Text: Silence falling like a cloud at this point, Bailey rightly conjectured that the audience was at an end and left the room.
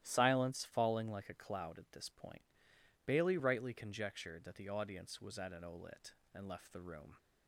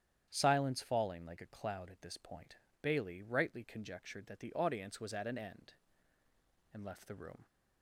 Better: second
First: starts louder than the rest; strong; until 1.0 s; 13.5 dB // says "olit" for "end"; at 5.6 s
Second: starts louder than the rest; strong; until 1.3 s; 9.5 dB

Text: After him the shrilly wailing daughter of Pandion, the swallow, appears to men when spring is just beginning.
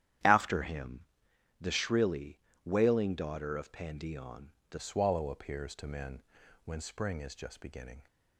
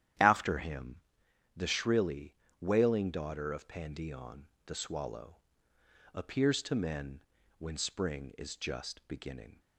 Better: second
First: starts louder than the rest; strong; until 1.8 s; 11 dB // pauses between "him" and "the"; noticeable; at 1.0 s; 0.56 s long // pauses between "shrilly" and "wailing"; slight; at 2.3 s; 0.26 s long // changes voice at "swallow"; from 4.7 s on; 3.3 s long // pauses between "men" and "when"; at 6.2 s; 0.42 s long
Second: starts louder than the rest; strong; until 1.7 s; 11 dB // pauses between "him" and "the"; noticeable; at 0.9 s; 0.56 s long // pauses between "shrilly" and "wailing"; slight; at 2.3 s; 0.26 s long // pauses between "men" and "when"; at 7.2 s; 0.37 s long

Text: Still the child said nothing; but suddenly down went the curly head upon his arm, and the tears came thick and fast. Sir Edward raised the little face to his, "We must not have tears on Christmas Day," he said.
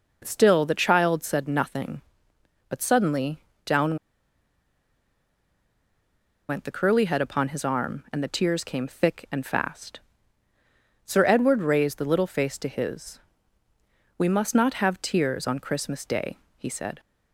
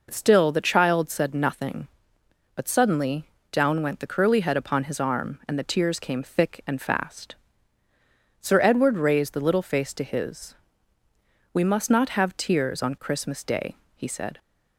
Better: second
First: pauses between "suddenly" and "down"; slight; at 3.3 s; 0.26 s long // pauses between "down" and "went"; strong; at 3.9 s; 2.5 s long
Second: pauses between "suddenly" and "down"; slight; at 3.2 s; 0.26 s long

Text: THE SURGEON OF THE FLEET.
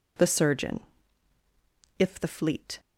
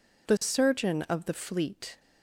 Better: second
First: says "If" for "OF"; at 1.9 s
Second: none

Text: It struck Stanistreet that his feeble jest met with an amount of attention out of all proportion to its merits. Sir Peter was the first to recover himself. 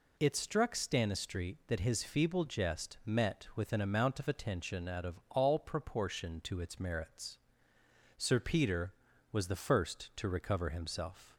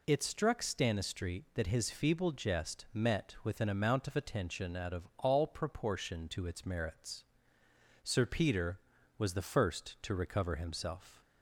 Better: neither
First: none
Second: none

